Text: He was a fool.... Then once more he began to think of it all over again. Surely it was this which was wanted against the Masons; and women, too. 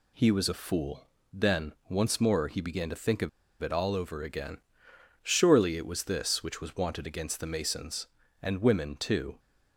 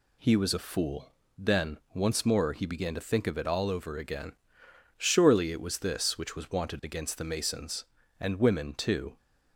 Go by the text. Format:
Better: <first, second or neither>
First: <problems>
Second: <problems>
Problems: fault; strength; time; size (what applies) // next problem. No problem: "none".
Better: second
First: pauses between "Then" and "once"; slight; at 1.7 s; 0.16 s long // pauses between "of" and "it"; slight; at 3.2 s; 0.33 s long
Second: pauses between "Then" and "once"; slight; at 1.7 s; 0.16 s long